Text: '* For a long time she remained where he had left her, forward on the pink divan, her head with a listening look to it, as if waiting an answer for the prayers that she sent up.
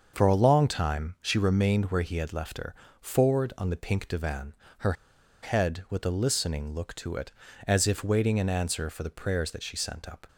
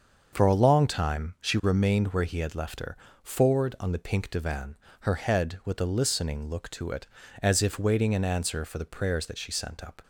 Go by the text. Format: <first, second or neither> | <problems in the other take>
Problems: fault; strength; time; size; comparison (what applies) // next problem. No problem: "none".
second | starts louder than the rest; until 1.1 s; 6.5 dB; also in the second // pauses between "her" and "head"; noticeable; at 4.9 s; 0.50 s long